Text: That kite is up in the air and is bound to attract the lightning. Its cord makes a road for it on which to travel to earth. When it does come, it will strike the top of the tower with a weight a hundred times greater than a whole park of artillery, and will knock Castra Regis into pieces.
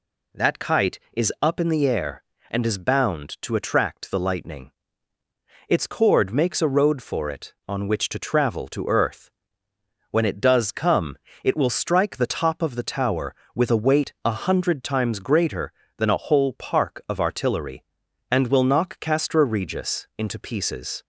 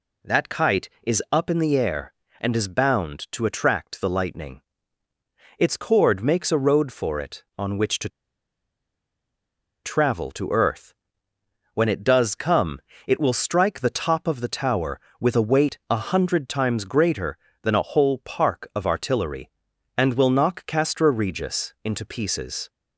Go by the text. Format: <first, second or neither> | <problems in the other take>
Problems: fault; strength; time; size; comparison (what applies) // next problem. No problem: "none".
first | pauses between "to" and "travel"; strong; at 8.0 s; 1.7 s long